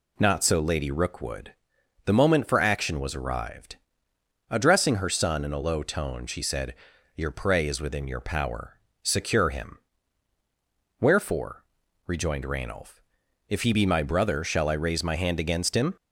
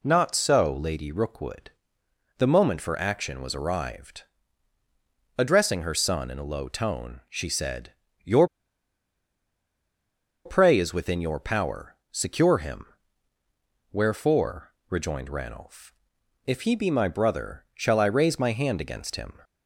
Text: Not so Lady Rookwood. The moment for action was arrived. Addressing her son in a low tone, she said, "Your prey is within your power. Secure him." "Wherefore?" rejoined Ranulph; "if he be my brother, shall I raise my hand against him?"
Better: first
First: none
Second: pauses between "Your" and "prey"; strong; at 8.4 s; 1.9 s long

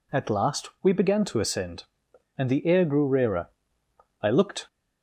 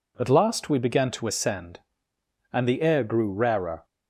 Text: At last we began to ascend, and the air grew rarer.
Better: second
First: goes on to say "I looked"; slight; from 4.2 s on; 0.44 s long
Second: none

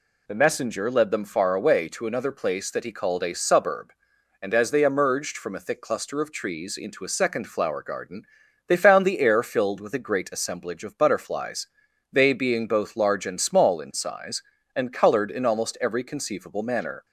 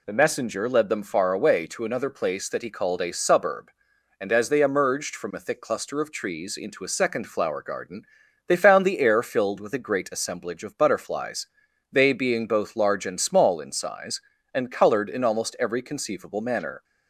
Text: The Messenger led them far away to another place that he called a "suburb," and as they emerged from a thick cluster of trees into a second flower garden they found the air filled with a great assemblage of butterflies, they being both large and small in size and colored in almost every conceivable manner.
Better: neither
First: pauses between "garden" and "they"; at 8.2 s; 0.42 s long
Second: pauses between "garden" and "they"; at 8.0 s; 0.42 s long

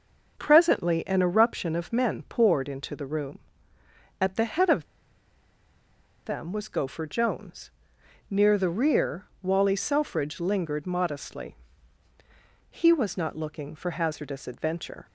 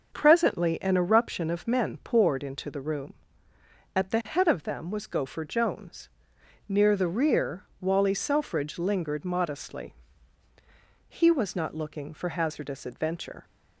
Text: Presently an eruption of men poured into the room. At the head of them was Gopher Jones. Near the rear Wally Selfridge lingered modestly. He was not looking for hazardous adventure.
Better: second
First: starts louder than the rest; until 1.4 s; 6.5 dB // pauses between "of" and "them"; strong; at 4.8 s; 1.4 s long // pauses between "rear" and "Wally"; slight; at 9.2 s; 0.18 s long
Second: starts louder than the rest; until 1.1 s; 6.5 dB // pauses between "rear" and "Wally"; slight; at 7.6 s; 0.18 s long

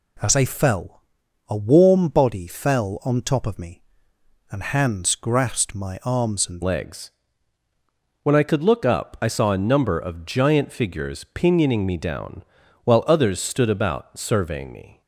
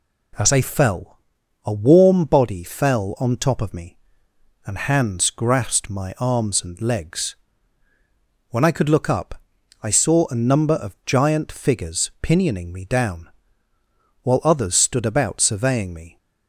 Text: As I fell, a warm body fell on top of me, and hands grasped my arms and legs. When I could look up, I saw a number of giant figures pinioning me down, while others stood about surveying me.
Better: second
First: changes voice at "legs"; from 6.6 s on; 8.4 s long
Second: none

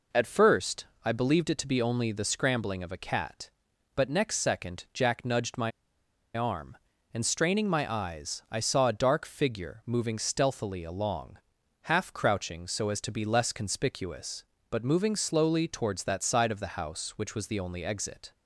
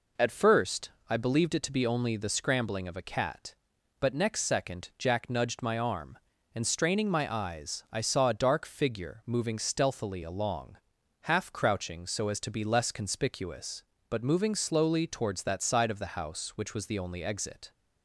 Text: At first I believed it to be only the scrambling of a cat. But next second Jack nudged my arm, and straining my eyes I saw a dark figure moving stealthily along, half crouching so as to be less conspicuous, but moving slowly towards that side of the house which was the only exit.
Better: second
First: pauses between "first" and "I"; slight; at 0.8 s; 0.18 s long // pauses between "my" and "arm"; noticeable; at 5.7 s; 0.65 s long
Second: pauses between "first" and "I"; slight; at 0.9 s; 0.18 s long

